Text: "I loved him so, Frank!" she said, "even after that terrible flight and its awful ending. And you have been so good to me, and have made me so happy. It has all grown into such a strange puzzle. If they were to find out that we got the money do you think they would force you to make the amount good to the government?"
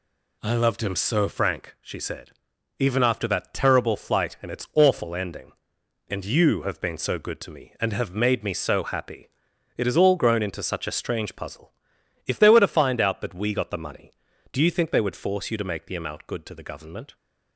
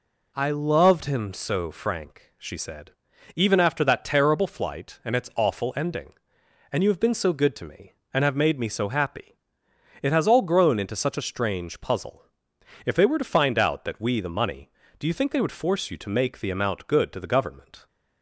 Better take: first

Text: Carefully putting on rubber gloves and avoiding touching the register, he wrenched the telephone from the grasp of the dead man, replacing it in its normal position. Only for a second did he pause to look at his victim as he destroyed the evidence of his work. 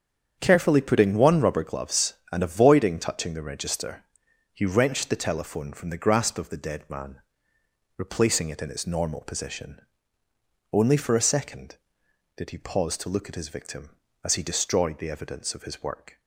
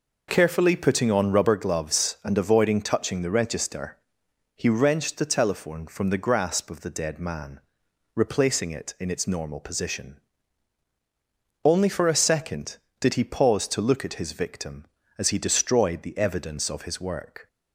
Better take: second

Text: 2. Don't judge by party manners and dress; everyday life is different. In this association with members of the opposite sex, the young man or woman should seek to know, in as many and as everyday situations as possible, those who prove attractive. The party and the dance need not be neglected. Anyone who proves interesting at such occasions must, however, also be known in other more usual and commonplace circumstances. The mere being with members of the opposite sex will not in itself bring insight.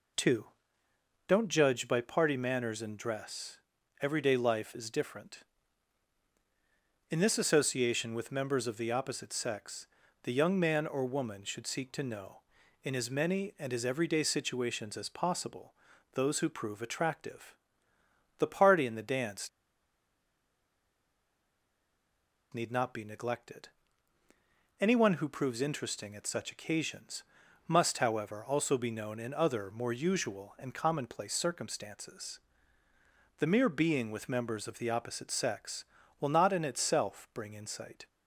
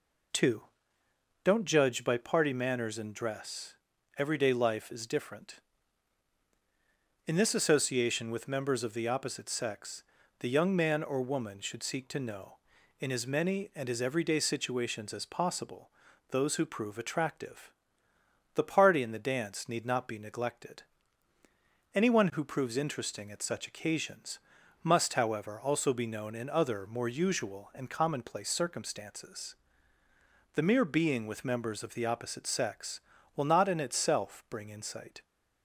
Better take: second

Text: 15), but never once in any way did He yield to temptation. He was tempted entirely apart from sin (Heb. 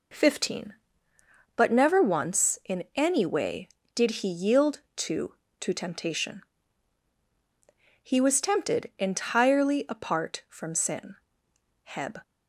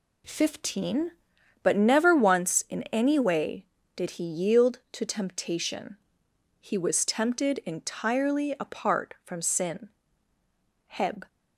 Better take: second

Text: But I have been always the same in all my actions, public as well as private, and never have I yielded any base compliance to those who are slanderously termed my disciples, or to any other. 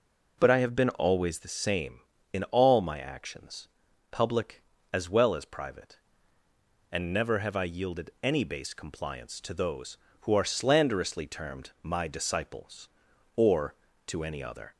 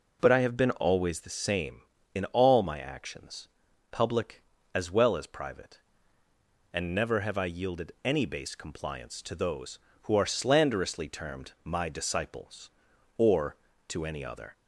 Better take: neither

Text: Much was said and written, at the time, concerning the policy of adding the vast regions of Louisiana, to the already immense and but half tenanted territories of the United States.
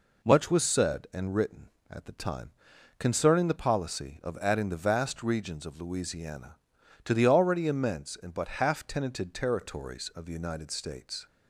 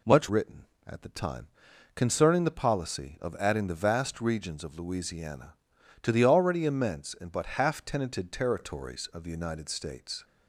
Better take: first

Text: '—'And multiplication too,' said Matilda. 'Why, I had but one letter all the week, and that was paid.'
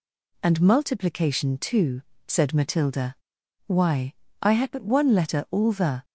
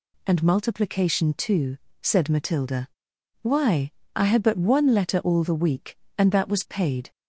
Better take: second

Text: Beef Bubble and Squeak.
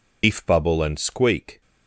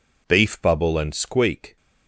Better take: second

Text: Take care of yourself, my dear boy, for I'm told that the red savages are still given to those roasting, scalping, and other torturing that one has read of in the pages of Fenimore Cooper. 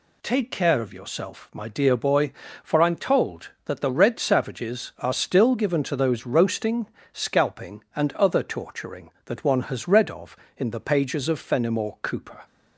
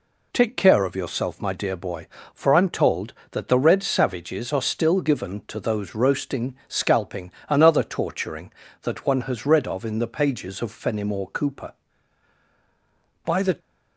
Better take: first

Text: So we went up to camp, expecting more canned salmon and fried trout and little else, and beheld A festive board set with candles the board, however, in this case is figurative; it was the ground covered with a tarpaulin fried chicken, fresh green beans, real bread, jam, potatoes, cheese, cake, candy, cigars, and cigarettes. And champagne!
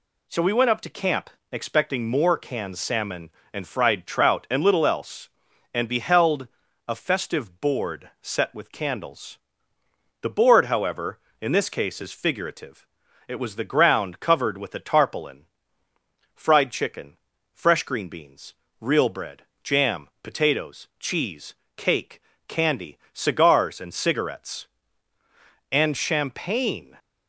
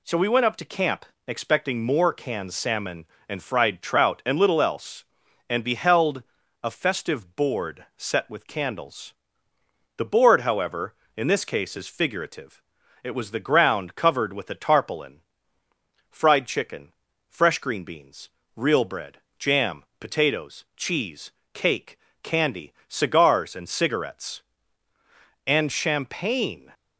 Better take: neither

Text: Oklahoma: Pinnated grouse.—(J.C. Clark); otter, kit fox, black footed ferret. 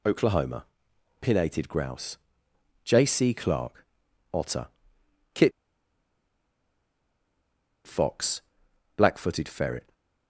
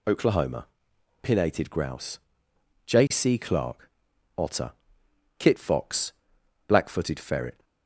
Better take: second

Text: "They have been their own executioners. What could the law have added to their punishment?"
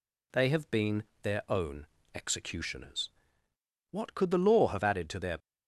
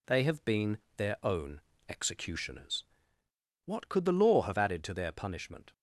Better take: second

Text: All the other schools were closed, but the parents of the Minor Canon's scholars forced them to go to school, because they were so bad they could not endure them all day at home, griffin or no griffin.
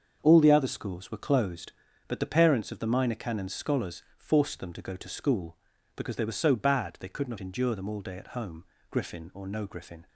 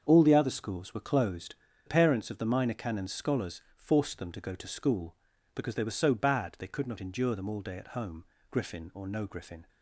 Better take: first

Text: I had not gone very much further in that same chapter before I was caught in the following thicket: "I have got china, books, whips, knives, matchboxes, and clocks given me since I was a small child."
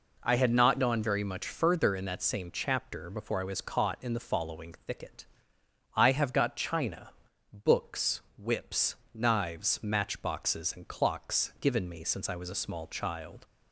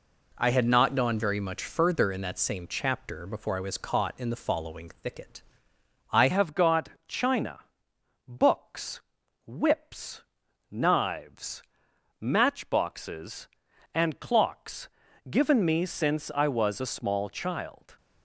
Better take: first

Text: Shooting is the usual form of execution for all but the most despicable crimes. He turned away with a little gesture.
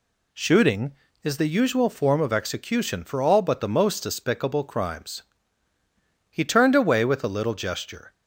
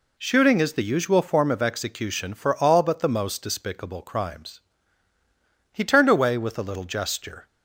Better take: neither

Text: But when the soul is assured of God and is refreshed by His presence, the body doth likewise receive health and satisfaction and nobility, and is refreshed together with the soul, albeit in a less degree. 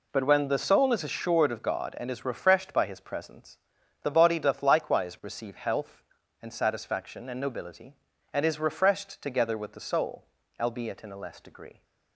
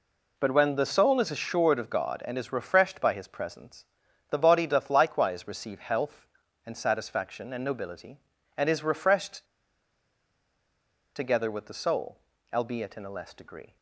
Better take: first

